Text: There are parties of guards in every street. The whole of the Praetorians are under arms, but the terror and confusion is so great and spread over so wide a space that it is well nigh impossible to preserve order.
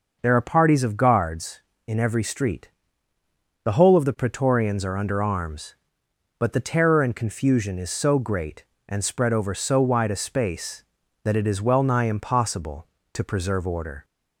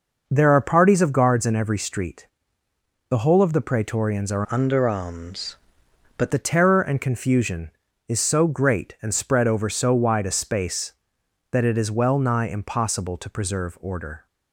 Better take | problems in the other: first | changes voice from "under" to "but"; from 4.4 to 6.3 s; 1.9 s long

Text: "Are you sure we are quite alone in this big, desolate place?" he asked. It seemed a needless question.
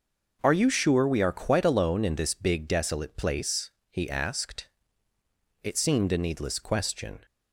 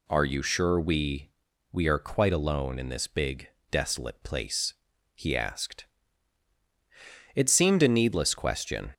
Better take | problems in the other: first | says "we" twice; at 1.7 s

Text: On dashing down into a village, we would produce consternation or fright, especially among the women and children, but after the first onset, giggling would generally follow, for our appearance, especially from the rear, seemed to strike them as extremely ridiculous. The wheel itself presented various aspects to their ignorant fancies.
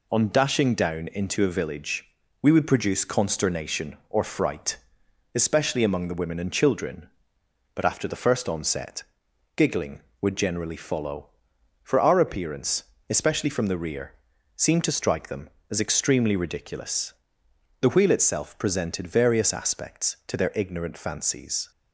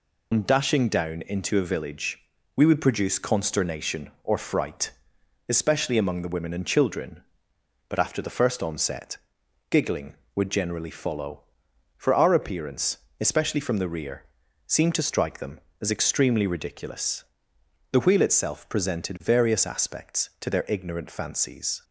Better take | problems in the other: first | loses the start of "On"; at 0.3 s; 85 ms

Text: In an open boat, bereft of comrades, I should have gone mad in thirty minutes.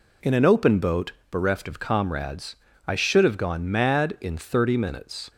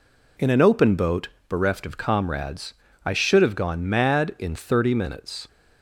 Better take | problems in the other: neither | none

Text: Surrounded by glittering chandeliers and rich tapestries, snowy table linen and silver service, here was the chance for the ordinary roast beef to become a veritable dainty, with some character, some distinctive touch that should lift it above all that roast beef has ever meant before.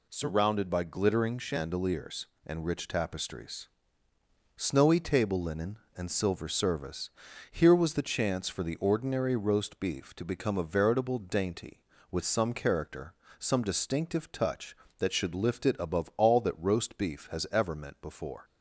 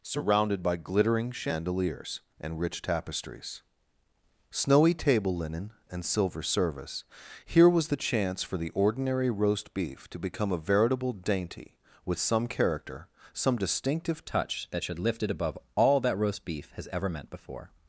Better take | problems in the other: first | changes voice at "touch"; from 14.2 s on; 3.5 s long // pauses between "above" and "all"; slight; at 15.5 s; 0.18 s long

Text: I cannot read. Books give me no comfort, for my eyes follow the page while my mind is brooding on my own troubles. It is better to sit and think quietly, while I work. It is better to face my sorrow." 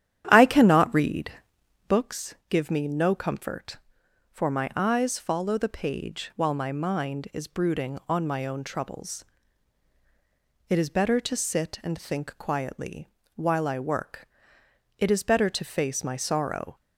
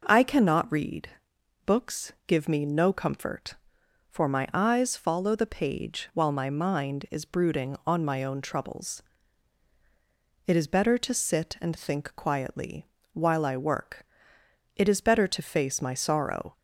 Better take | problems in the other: second | starts louder than the rest; strong; until 2.0 s; 10.5 dB // pauses between "Books" and "give"; slight; at 2.3 s; 0.16 s long; slight in the second

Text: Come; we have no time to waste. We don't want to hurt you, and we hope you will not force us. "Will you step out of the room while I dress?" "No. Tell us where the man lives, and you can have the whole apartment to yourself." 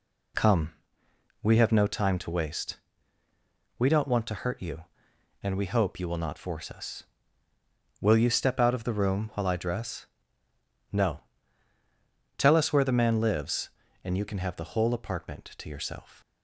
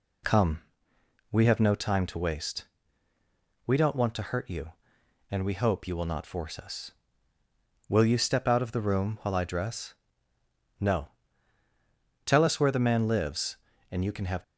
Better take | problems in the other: first | stops before "the whole apartment to yourself"; at 14.4 s

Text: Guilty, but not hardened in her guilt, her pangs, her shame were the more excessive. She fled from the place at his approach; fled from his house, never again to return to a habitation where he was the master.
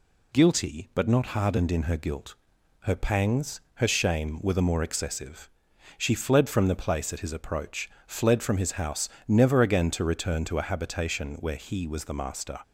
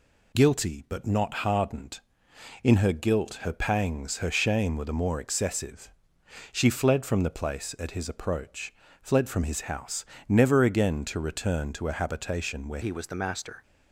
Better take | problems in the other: first | changes voice at "he"; from 12.8 s on; 0.8 s long

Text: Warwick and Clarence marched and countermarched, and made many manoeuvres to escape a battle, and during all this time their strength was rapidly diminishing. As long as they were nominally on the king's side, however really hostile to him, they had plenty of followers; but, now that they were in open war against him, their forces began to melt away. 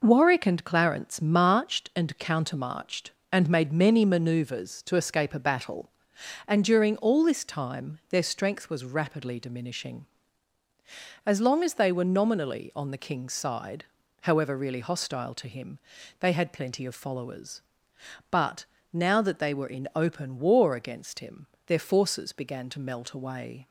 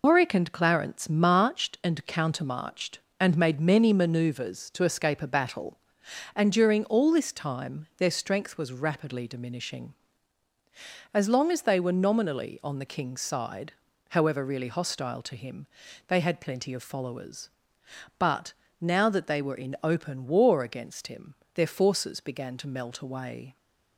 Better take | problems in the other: first | loses the start of "Warwick"; at 0.0 s; 145 ms

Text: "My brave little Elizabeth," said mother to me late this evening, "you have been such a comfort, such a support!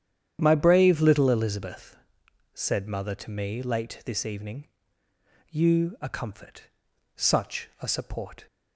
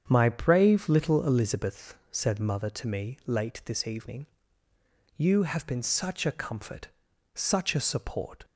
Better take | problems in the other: second | starts louder than the rest; strong; until 1.4 s; 9.5 dB; strong in the second // skips "have been such"; at 5.9 s

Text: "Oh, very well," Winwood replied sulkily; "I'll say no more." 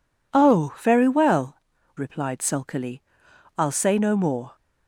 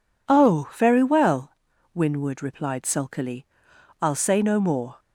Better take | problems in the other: second | skips "Winwood"; at 1.7 s

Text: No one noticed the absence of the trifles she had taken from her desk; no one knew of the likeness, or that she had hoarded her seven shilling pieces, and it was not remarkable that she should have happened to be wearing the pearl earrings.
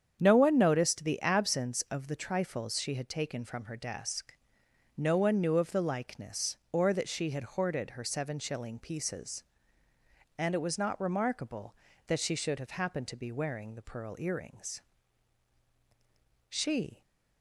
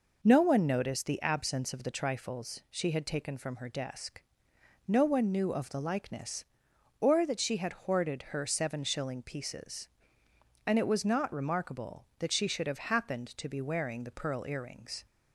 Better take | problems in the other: second | starts louder than the rest; strong; until 1.2 s; 8 dB // goes on to say "She"; from 16.4 s on; 0.54 s long

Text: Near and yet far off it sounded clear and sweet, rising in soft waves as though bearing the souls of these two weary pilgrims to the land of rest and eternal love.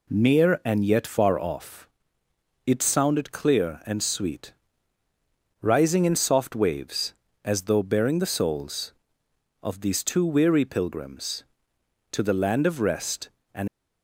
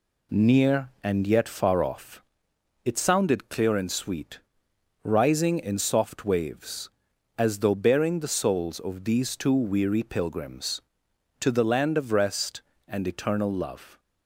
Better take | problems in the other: second | pauses between "off" and "it"; noticeable; at 1.8 s; 0.78 s long; noticeable in the second // stops before "eternal love"; at 13.6 s

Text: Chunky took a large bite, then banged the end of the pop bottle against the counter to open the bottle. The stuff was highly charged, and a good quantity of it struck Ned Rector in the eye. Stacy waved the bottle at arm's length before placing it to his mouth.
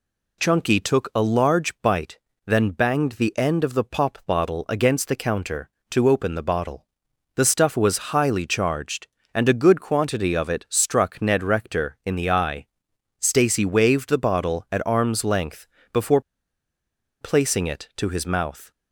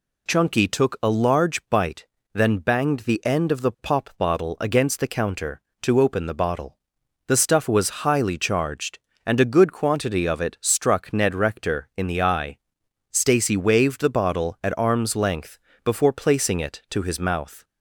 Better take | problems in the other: second | pauses between "length" and "before"; slight; at 15.6 s; 0.26 s long; slight in the second // pauses between "before" and "placing"; at 16.2 s; 1.0 s long

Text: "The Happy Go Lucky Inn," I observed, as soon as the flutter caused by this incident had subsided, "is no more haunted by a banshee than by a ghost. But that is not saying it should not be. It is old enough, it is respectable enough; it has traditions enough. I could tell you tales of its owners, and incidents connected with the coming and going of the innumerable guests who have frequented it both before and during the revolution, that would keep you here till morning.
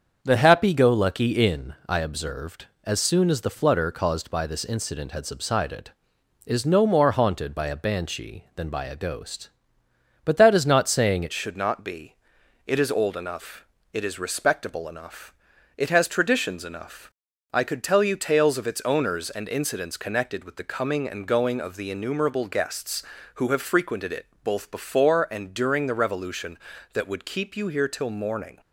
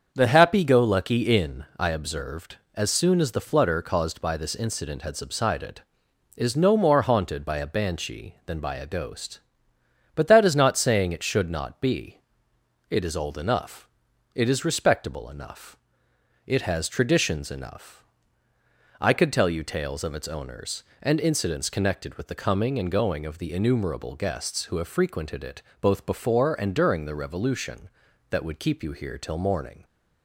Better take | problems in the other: second | starts louder than the rest; until 1.2 s; 7 dB; also in the second // changes voice at "should"; from 11.3 s on; 17.3 s long // pauses between "it" and "both"; slight; at 24.2 s; 0.18 s long; slight in the second

